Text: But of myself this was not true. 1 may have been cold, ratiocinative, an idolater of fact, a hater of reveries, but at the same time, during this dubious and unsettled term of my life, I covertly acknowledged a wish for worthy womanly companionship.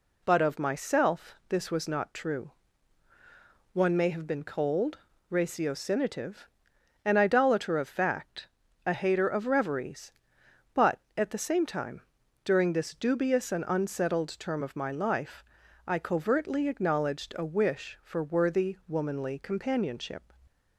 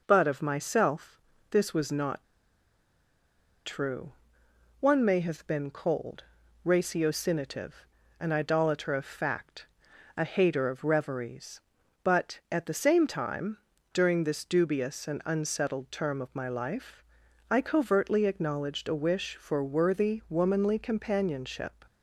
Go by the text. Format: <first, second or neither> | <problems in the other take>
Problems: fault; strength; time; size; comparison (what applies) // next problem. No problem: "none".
first | pauses between "myself" and "this"; slight; at 1.1 s; 0.32 s long // pauses between "not" and "true"; strong; at 2.2 s; 1.4 s long